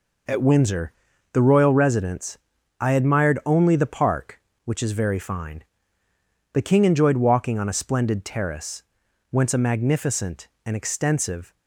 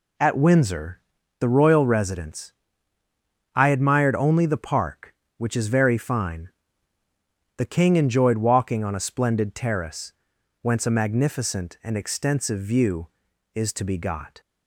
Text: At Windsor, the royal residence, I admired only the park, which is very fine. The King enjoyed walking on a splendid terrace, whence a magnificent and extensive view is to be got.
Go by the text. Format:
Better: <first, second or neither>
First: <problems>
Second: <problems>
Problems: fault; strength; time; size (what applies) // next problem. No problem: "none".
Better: second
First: stops before "view is to be got"; at 11.5 s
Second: none